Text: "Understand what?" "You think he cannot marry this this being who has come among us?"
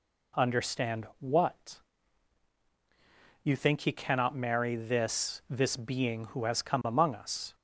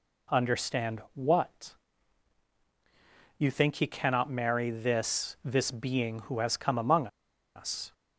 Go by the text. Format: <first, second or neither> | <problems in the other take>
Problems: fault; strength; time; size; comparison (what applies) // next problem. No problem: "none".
first | pauses between "among" and "us"; noticeable; at 7.0 s; 0.48 s long